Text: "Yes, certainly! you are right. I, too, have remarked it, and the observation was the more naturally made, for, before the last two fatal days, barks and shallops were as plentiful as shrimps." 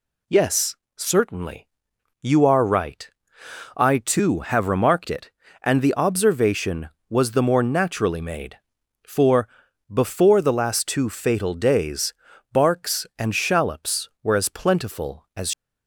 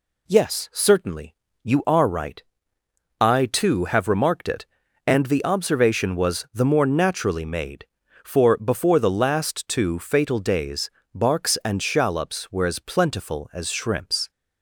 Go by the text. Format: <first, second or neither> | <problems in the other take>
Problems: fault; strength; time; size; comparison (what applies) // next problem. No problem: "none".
second | stops before "shrimps"; at 15.5 s